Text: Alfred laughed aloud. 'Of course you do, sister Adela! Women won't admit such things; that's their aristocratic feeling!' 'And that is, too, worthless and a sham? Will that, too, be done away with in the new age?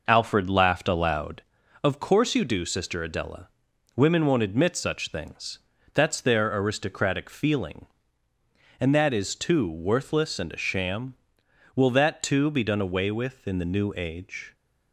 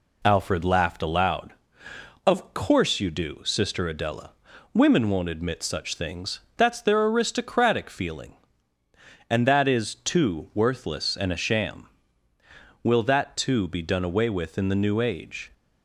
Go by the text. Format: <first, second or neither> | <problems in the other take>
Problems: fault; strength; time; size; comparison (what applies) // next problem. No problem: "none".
second | starts louder than the rest; noticeable; until 1.5 s; 5 dB